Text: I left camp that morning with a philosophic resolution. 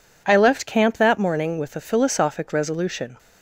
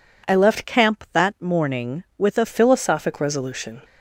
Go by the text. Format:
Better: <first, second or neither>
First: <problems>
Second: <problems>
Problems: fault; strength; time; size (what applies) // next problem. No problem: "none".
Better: first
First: none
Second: changes voice from "camp" to "a"; from 0.6 to 2.4 s; 1.8 s long